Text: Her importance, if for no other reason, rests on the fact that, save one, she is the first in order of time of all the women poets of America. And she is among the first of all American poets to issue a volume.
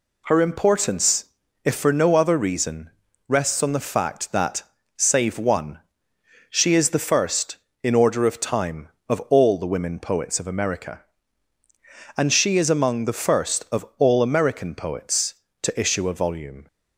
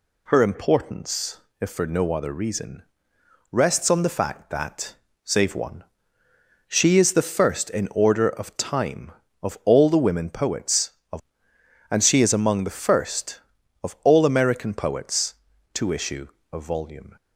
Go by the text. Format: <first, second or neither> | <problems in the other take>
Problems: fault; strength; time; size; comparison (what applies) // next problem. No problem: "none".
first | skips "America"; at 11.5 s // pauses between "issue" and "a"; slight; at 16.2 s; 0.26 s long